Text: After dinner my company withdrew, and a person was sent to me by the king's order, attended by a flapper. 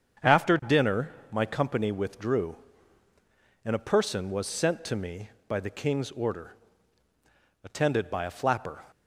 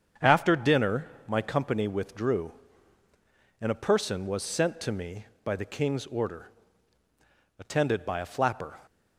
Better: neither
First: starts louder than the rest; strong; until 1.4 s; 7.5 dB // pauses between "dinner" and "my"; slight; at 1.1 s; 0.20 s long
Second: starts louder than the rest; strong; until 1.4 s; 7.5 dB // pauses between "dinner" and "my"; slight; at 1.0 s; 0.20 s long

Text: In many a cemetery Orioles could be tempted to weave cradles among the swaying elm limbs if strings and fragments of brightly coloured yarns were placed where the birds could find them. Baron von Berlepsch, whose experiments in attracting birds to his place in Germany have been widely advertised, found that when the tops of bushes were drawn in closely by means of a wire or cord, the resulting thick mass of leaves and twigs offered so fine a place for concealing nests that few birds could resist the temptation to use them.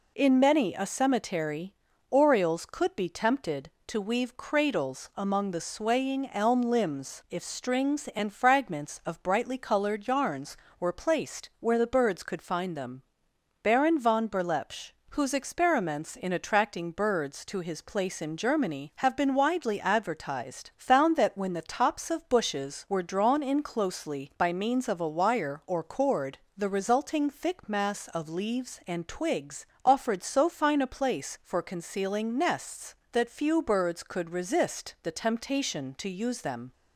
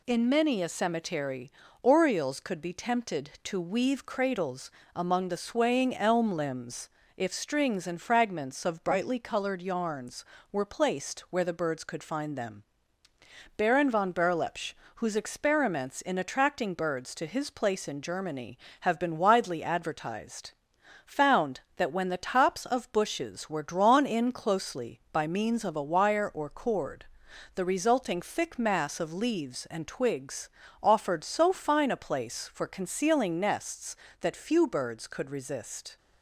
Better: first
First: pauses between "cemetery" and "Orioles"; at 1.7 s; 0.38 s long // pauses between "twigs" and "offered"; slight; at 29.6 s; 0.18 s long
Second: pauses between "cemetery" and "Orioles"; slight; at 1.4 s; 0.32 s long // pauses between "cradles" and "among"; slight; at 4.6 s; 0.28 s long // pauses between "limbs" and "if"; slight; at 6.8 s; 0.28 s long // pauses between "twigs" and "offered"; slight; at 30.5 s; 0.32 s long // stops before "the temptation to use them"; at 35.9 s

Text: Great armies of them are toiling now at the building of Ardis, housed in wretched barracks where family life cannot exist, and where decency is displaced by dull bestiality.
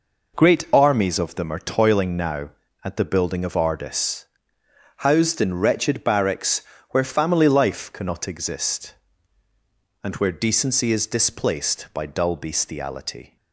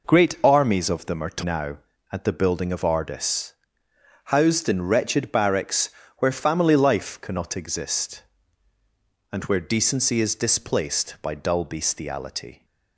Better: first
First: pauses between "barracks" and "where"; slight; at 6.6 s; 0.30 s long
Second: skips "toiling"; at 1.4 s // pauses between "barracks" and "where"; slight; at 5.8 s; 0.30 s long

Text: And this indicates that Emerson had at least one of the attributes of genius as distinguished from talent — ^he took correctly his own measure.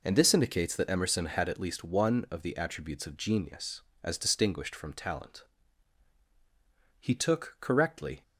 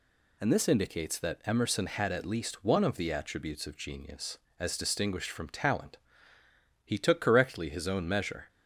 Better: second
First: stops before "his own measure"; at 8.2 s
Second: none

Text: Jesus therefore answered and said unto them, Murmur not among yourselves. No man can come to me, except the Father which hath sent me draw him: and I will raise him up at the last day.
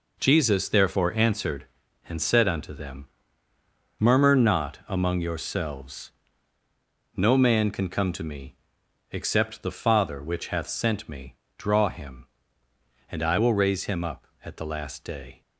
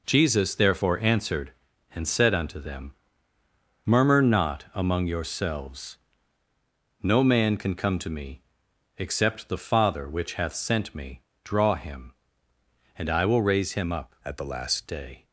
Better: first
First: pauses between "me" and "draw"; slight; at 11.3 s; 0.20 s long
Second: pauses between "me" and "draw"; slight; at 11.2 s; 0.20 s long // changes voice from "at" to "last"; from 14.2 to 14.8 s; 0.6 s long

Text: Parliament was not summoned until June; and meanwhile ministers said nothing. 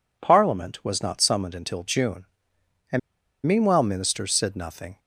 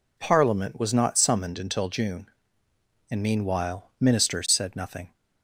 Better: second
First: pauses between "and" and "meanwhile"; noticeable; at 2.9 s; 0.46 s long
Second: none

